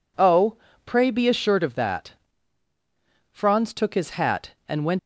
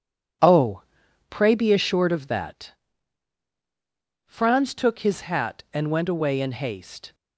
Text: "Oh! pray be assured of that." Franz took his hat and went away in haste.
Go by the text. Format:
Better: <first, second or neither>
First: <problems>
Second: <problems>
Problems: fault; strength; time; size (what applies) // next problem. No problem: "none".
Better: second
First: stops before "away in haste"; at 4.9 s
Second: none